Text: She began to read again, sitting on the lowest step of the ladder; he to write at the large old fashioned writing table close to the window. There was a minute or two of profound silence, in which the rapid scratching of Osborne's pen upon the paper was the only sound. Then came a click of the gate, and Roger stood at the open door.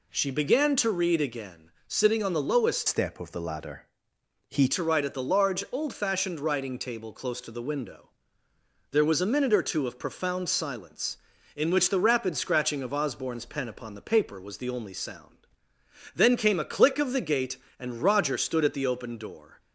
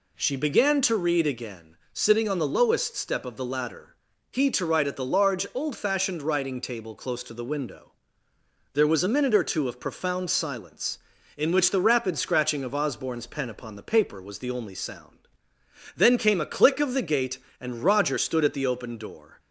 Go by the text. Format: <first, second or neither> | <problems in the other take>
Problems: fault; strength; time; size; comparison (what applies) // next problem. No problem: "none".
second | changes voice from "step" to "he"; from 2.8 to 4.6 s; 1.8 s long